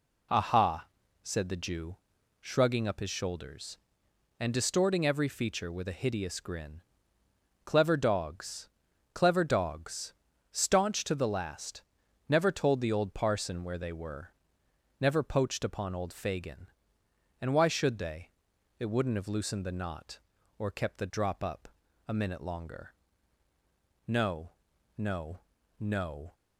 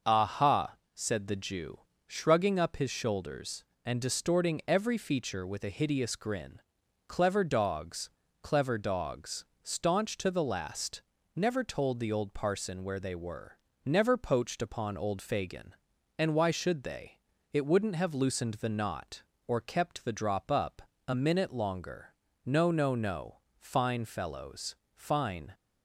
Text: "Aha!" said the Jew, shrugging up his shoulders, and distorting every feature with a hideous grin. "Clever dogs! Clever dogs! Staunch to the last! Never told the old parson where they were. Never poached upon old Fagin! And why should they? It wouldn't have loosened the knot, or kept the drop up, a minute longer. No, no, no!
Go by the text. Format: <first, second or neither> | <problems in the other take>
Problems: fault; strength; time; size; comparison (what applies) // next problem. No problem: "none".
first | starts louder than the rest; until 1.2 s; 6 dB // goes on to say "Fine fellows Fine"; strong; from 23.5 s on; 1.9 s long